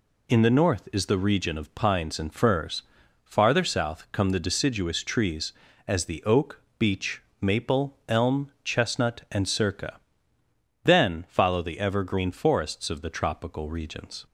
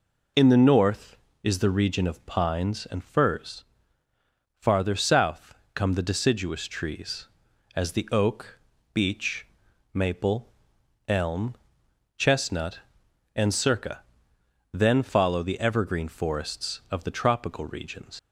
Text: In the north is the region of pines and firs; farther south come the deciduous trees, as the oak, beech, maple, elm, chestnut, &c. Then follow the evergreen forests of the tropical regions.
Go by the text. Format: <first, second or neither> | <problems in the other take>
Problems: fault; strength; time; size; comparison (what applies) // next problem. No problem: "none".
first | pauses between "south" and "come"; slight; at 5.5 s; 0.20 s long // leaves "regions" unfinished; at 18.1 s; 110 ms